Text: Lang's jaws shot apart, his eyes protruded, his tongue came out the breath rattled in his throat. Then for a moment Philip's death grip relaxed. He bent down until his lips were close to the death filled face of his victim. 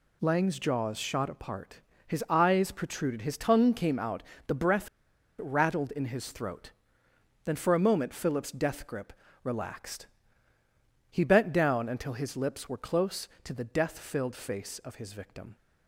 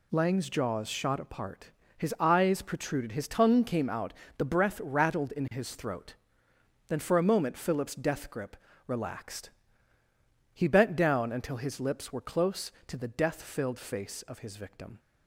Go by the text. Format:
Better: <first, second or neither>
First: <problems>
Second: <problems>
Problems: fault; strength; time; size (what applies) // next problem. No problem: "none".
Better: second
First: pauses between "out" and "the"; slight; at 4.2 s; 0.26 s long // pauses between "breath" and "rattled"; noticeable; at 4.8 s; 0.53 s long // pauses between "grip" and "relaxed"; slight; at 9.1 s; 0.30 s long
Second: pauses between "out" and "the"; slight; at 4.1 s; 0.26 s long // pauses between "grip" and "relaxed"; slight; at 8.5 s; 0.30 s long